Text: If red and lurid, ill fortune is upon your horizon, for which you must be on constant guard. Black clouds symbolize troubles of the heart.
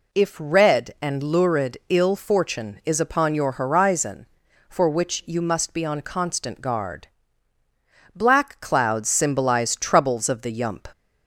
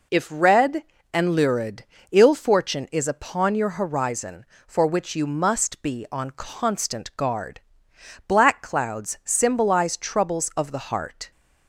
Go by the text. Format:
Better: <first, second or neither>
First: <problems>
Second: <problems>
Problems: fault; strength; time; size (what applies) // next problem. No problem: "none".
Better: second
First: says "yump" for "heart"; at 10.5 s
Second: none